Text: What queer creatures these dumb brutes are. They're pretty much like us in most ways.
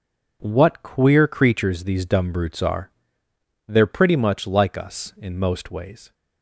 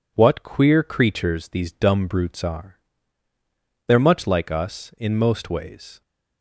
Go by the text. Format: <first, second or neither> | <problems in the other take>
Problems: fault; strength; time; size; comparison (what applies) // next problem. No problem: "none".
first | skips "pretty"; at 3.9 s